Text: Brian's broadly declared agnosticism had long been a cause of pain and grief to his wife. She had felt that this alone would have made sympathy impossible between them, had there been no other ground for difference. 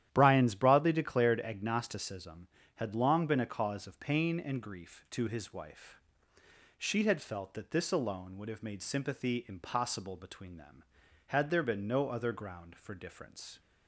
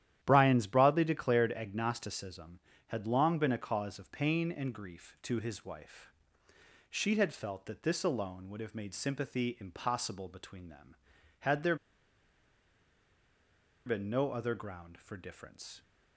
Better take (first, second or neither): first